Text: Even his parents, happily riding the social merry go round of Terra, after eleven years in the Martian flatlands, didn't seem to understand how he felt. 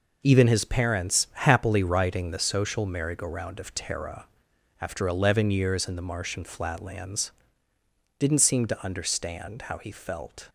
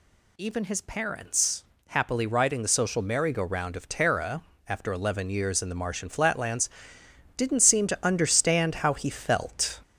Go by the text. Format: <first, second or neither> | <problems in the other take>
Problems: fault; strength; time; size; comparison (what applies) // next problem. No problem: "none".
first | gets louder; slight; throughout; 3 dB